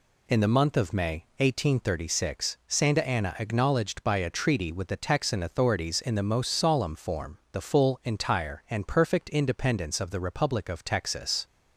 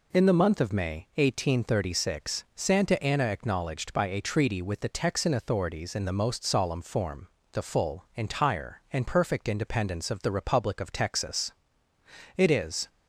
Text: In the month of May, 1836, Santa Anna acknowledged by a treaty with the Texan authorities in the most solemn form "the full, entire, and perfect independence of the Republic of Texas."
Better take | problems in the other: first | pauses between "form" and "the"; slight; at 7.2 s; 0.24 s long // goes on to say "It is"; from 12.3 s on; 0.52 s long

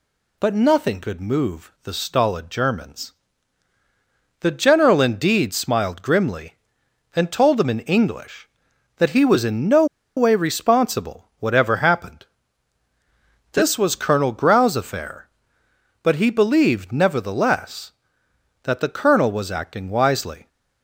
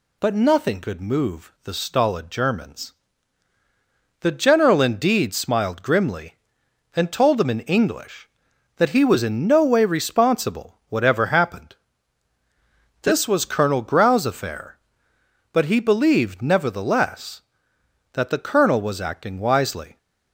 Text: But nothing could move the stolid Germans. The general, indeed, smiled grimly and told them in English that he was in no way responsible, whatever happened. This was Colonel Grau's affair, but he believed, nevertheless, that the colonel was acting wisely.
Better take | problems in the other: second | pauses between "no" and "way"; slight; at 9.8 s; 0.31 s long

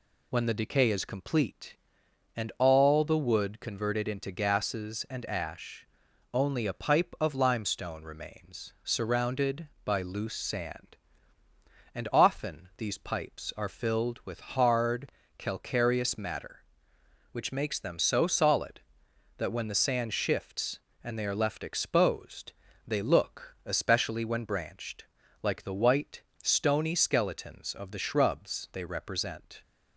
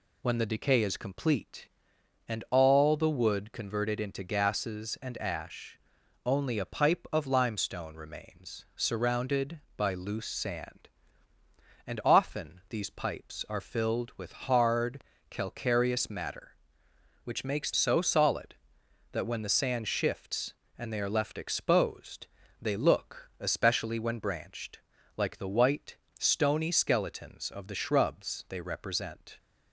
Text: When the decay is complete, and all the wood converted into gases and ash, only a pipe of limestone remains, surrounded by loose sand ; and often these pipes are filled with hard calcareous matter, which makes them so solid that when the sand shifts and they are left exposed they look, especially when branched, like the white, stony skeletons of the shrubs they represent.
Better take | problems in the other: first | pauses between "hard" and "calcareous"; slight; at 15.0 s; 0.28 s long; slight in the first // skips "them"; at 17.7 s // pauses between "exposed" and "they"; slight; at 22.2 s; 0.34 s long; slight in the first

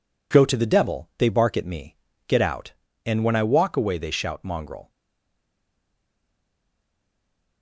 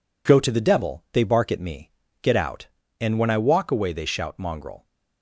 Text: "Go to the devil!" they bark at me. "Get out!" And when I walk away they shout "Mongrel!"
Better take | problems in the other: second | stays silent after the last word; strong; from 4.8 s on; 2.8 s long

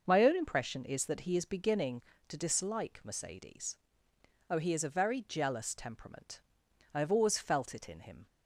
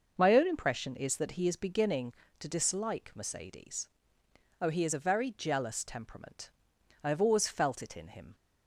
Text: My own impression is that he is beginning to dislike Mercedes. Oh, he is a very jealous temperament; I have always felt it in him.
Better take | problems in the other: neither | none

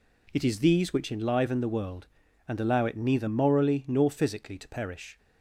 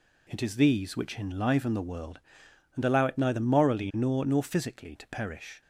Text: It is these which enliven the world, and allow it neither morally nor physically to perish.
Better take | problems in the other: first | says "nor" twice; at 4.2 s

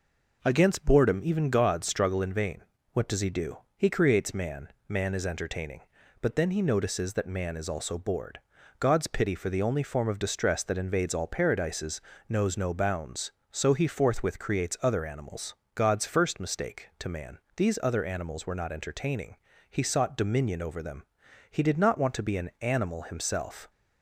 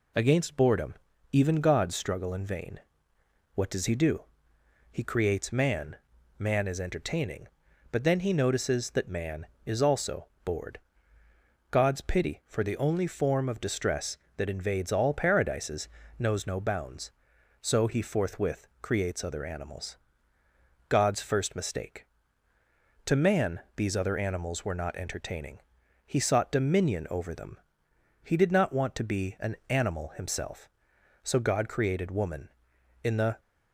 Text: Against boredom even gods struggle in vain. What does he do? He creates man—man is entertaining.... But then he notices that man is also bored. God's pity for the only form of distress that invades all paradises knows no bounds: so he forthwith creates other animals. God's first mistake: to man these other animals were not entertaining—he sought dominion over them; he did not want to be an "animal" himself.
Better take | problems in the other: first | pauses between "boredom" and "even"; slight; at 0.9 s; 0.36 s long // pauses between "also" and "bored"; slight; at 10.2 s; 0.18 s long // pauses between "paradises" and "knows"; slight; at 15.8 s; 0.32 s long; slight in the first // pauses between "forthwith" and "creates"; slight; at 18.6 s; 0.16 s long // pauses between "man" and "these"; slight; at 23.5 s; 0.16 s long; slight in the first // goes on to say "So God created woman In the"; strong; from 31.2 s on; 2.1 s long

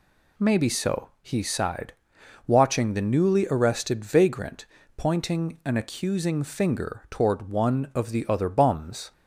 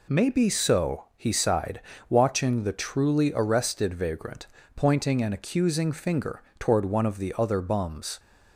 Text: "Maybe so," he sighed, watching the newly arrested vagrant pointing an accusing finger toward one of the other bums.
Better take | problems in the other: first | says "truly" for "newly"; at 2.7 s // pauses between "vagrant" and "pointing"; slight; at 4.4 s; 0.28 s long; slight in the first // pauses between "finger" and "toward"; slight; at 6.4 s; 0.16 s long

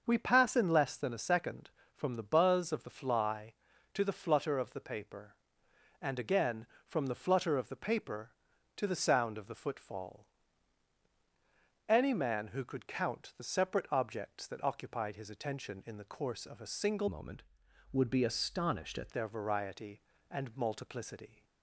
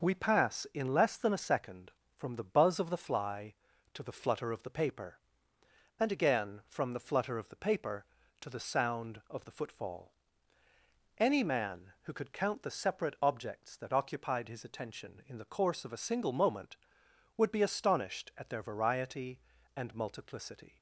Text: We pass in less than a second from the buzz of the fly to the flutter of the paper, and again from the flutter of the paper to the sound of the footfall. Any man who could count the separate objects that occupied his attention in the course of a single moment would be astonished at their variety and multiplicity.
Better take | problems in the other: second | starts louder than the rest; until 1.0 s; 6.5 dB // changes voice from "moment" to "at"; from 17.0 to 19.0 s; 2.0 s long

